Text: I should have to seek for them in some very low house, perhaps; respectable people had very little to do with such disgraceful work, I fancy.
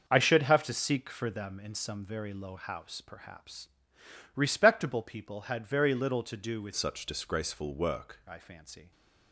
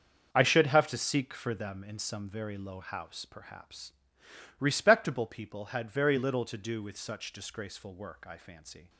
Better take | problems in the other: second | starts louder than the rest; until 1.1 s; 6.5 dB; also in the second // changes voice from "such" to "work"; from 6.7 to 8.1 s; 1.4 s long

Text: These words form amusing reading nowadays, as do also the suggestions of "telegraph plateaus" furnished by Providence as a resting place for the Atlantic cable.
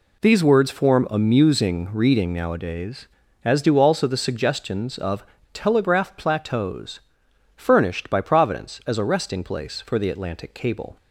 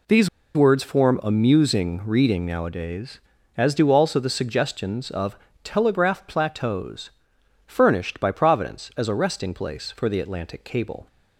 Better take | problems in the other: first | pauses between "These" and "words"; slight; at 0.2 s; 0.26 s long // pauses between "of" and "telegraph"; slight; at 5.3 s; 0.30 s long; slight in the first // pauses between "plateaus" and "furnished"; noticeable; at 7.1 s; 0.56 s long; noticeable in the first

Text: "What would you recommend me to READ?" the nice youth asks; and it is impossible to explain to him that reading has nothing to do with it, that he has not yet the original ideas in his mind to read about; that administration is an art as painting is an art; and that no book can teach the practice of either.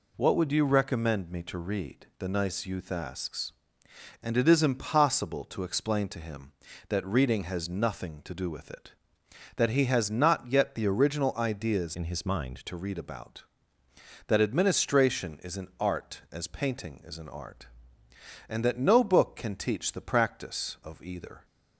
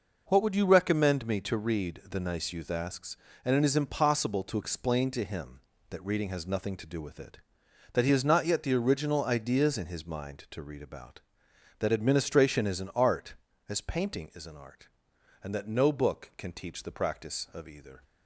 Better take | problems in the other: second | changes voice from "in" to "mind"; from 11.9 to 12.6 s; 0.7 s long

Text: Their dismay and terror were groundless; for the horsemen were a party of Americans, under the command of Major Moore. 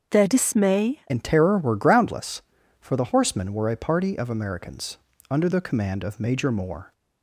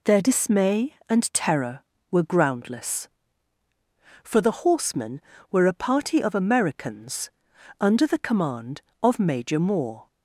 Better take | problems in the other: second | starts louder than the rest; until 1.1 s; 6.5 dB // changes voice at "and"; from 1.0 s on; 5.9 s long

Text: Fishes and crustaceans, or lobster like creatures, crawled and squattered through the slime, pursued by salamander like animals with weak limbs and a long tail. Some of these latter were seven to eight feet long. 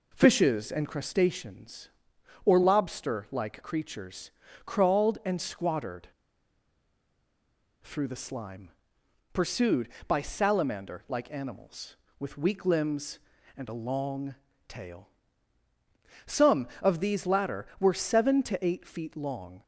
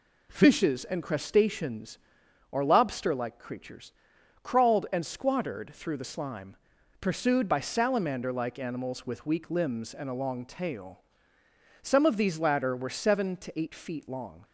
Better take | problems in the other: second | pauses between "squattered" and "through"; strong; at 6.0 s; 1.7 s long // pauses between "long" and "tail"; slight; at 14.3 s; 0.34 s long

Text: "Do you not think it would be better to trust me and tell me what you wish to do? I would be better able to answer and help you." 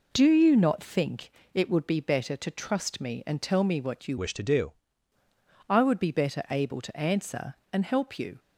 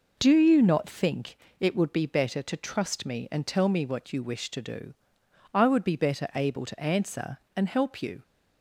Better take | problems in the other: second | pauses between "think" and "it"; slight; at 1.3 s; 0.22 s long; slight in the second // changes voice from "wish" to "do"; from 4.1 to 4.7 s; 0.6 s long

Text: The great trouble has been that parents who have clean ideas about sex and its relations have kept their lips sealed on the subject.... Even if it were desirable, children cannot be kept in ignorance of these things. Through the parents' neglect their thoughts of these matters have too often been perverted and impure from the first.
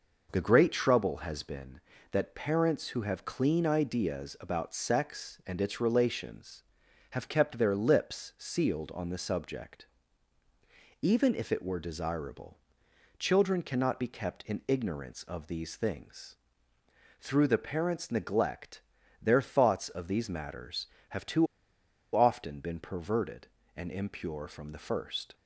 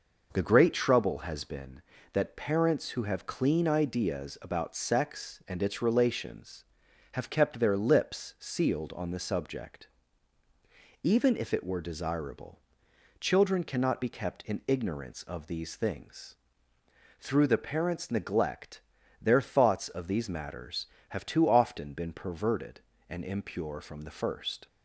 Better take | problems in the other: second | pauses between "neglect" and "their"; at 18.8 s; 0.40 s long; also in the second // pauses between "too" and "often"; noticeable; at 21.4 s; 0.68 s long

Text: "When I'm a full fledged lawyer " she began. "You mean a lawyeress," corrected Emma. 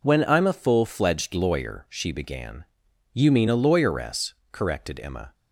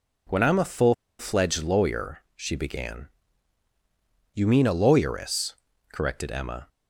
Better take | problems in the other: first | pauses between "full" and "fledged"; slight; at 0.9 s; 0.25 s long

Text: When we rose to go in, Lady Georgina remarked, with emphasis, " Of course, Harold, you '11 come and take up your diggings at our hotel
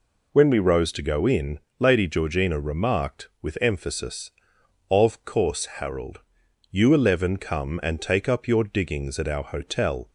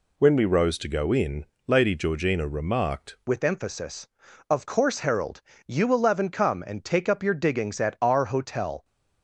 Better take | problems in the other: first | changes voice at "with"; from 3.2 s on; 5.6 s long

